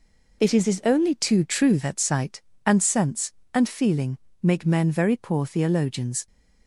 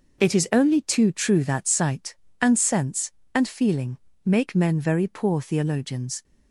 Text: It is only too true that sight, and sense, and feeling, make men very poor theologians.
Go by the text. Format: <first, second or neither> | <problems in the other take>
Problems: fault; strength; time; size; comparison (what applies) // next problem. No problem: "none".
second | says "is" twice; at 0.6 s